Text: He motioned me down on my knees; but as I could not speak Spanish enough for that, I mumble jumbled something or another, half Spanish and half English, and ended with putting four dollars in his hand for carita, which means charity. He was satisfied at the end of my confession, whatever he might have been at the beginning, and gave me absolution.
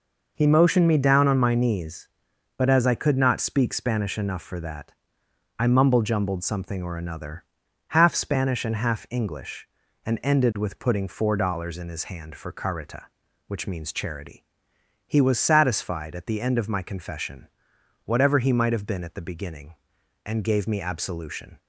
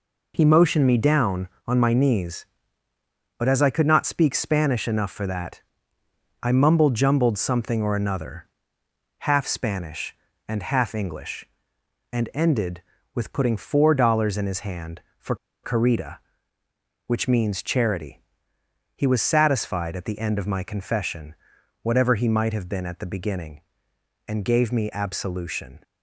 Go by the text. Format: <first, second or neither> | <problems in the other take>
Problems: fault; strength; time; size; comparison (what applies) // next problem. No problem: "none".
first | pauses between "for" and "carita"; slight; at 15.3 s; 0.28 s long